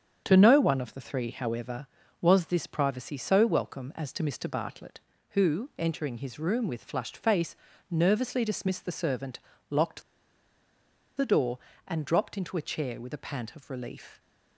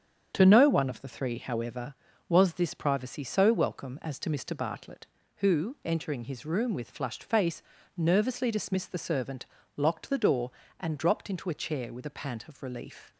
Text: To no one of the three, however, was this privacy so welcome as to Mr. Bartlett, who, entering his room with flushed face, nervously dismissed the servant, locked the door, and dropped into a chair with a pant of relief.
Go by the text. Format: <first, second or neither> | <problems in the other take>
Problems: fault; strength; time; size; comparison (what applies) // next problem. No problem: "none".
second | starts louder than the rest; strong; until 1.2 s; 7.5 dB; strong in the second // pauses between "locked" and "the"; at 10.0 s; 1.1 s long